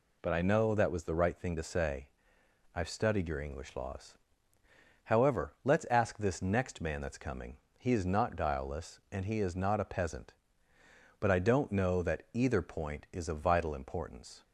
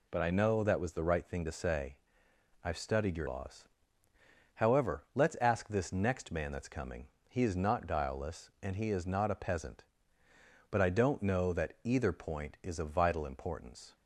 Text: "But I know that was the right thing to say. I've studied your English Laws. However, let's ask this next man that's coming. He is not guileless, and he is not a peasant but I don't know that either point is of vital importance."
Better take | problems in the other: first | skips "English"; at 3.2 s

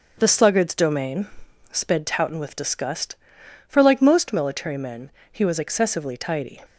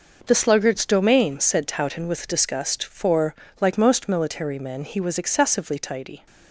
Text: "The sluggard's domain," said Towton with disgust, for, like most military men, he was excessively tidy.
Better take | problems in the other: second | starts louder than the rest; until 1.1 s; 6.5 dB // says "sped" for "said"; at 1.7 s

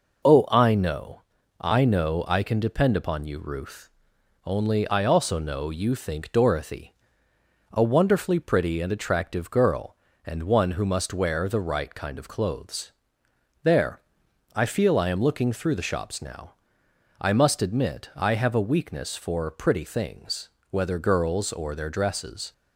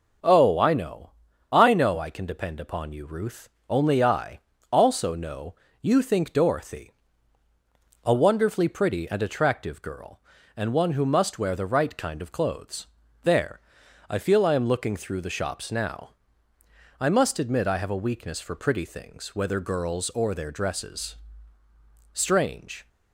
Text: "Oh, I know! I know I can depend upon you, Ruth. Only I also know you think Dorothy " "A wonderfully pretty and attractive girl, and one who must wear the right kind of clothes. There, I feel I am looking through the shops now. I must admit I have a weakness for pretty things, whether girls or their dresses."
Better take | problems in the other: first | starts louder than the rest; until 1.6 s; 6.5 dB // pauses between "I" and "also"; slight; at 4.4 s; 0.32 s long // pauses between "know" and "you"; slight; at 5.5 s; 0.26 s long // goes on to say "Strange"; noticeable; from 22.1 s on; 0.76 s long

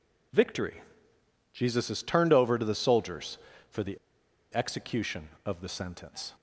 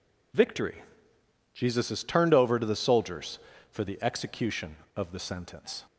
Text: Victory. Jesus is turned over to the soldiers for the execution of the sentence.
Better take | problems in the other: second | pauses between "the" and "execution"; noticeable; at 3.9 s; 0.57 s long

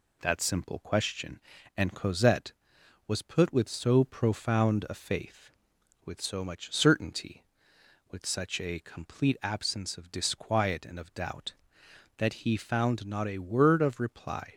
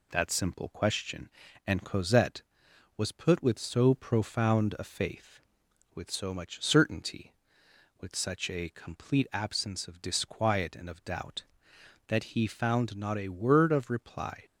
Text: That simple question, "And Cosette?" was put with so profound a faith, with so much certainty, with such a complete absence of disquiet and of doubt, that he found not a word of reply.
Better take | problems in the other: neither | none

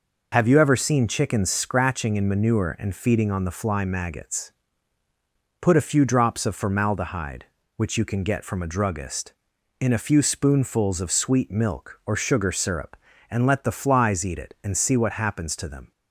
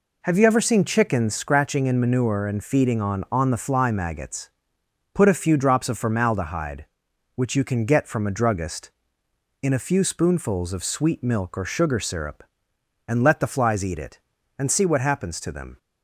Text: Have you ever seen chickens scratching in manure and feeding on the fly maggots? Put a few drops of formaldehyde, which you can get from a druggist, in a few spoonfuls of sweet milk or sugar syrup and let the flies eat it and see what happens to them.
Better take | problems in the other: first | says "on" twice; at 3.3 s

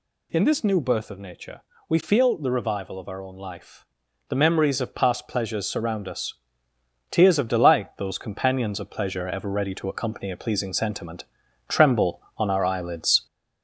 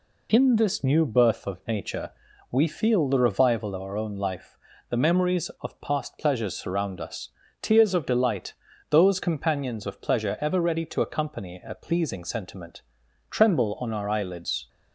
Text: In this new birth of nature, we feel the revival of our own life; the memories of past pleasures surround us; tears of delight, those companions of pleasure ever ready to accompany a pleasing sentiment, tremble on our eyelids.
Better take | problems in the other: second | gets louder; slight; throughout; 2 dB

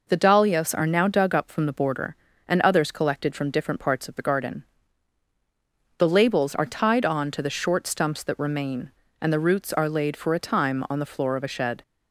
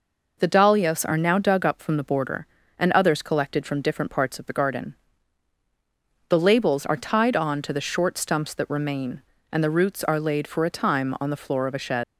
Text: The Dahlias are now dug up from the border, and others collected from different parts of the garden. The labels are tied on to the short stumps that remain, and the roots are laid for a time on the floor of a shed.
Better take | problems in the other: first | leaves "shed" unfinished; at 12.0 s; 90 ms

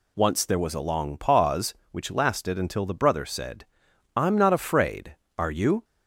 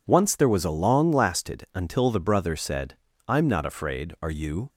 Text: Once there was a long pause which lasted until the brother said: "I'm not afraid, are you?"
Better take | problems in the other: first | skips "pause which"; at 1.1 s

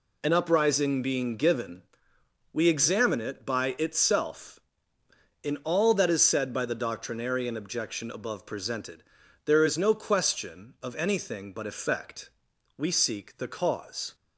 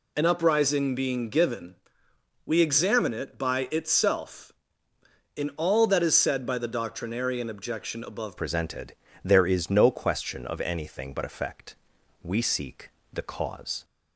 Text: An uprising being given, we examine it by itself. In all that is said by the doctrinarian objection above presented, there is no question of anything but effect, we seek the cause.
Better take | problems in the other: first | changes voice at "presented"; from 8.3 s on; 5.5 s long // pauses between "seek" and "the"; slight; at 12.9 s; 0.22 s long

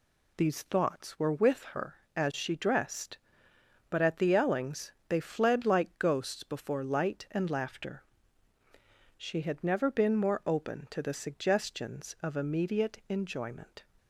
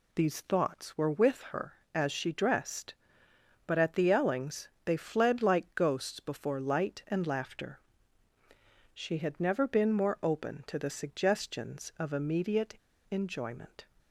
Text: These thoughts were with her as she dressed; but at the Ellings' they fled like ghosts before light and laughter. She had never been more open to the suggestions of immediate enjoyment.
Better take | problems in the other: first | pauses between "Ellings" and "they"; slight; at 4.6 s; 0.16 s long; slight in the first // pauses between "immediate" and "enjoyment"; slight; at 12.7 s; 0.31 s long

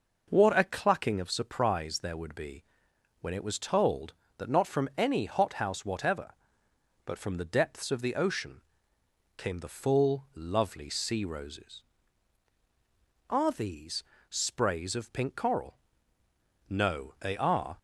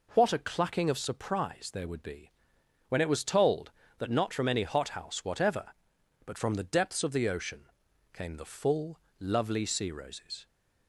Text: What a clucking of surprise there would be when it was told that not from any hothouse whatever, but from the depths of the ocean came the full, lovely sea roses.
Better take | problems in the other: second | pauses between "be" and "when"; noticeable; at 2.6 s; 0.58 s long; noticeable in the second // pauses between "ocean" and "came"; noticeable; at 8.5 s; 0.78 s long; noticeable in the second // goes on to say "Are these sprays of pink coral No they are"; strong; from 13.2 s on; 4.4 s long

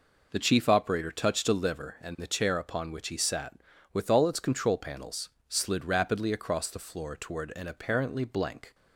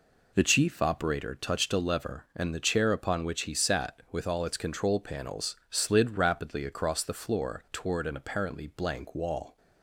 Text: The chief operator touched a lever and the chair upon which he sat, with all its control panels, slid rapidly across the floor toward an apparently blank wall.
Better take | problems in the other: second | stops before "wall"; at 8.7 s

